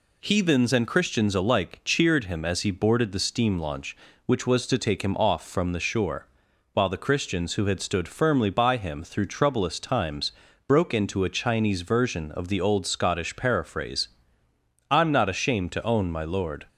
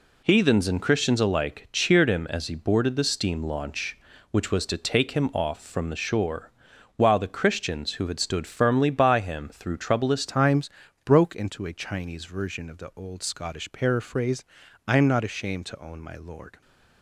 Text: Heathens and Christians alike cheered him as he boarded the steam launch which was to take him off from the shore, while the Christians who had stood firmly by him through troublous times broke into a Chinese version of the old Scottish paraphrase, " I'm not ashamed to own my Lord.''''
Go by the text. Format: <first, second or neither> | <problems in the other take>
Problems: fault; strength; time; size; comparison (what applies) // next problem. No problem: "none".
first | changes voice at "times"; from 10.2 s on; 6.4 s long // pauses between "times" and "broke"; slight; at 10.6 s; 0.36 s long; slight in the first